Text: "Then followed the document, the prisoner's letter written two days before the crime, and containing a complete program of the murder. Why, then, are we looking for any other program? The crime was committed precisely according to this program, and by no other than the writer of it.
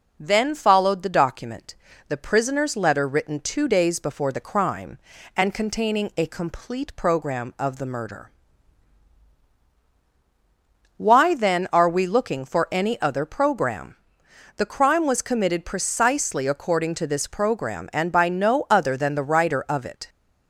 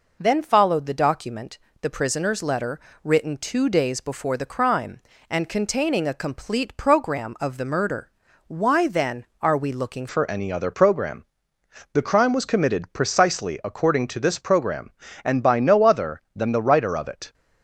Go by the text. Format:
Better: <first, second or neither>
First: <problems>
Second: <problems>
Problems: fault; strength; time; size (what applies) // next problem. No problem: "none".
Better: first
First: none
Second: pauses between "letter" and "written"; slight; at 2.8 s; 0.24 s long // changes voice at "for"; from 10.0 s on; 7.3 s long